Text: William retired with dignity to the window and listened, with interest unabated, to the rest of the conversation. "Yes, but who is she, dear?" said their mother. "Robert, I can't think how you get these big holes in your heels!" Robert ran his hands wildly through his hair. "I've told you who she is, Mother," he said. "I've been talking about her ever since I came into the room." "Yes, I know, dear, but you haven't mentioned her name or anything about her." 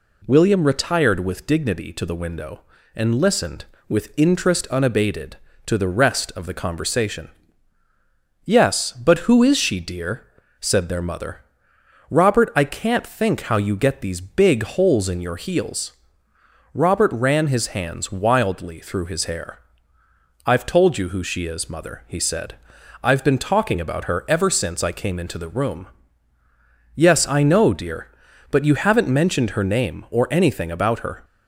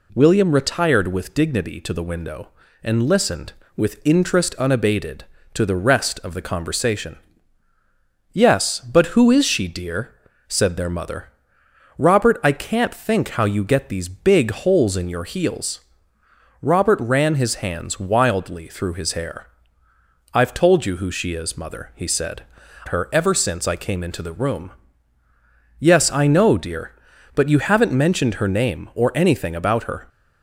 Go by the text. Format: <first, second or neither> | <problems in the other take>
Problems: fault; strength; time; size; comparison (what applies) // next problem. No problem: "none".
first | skips "I've been talking about"; at 22.6 s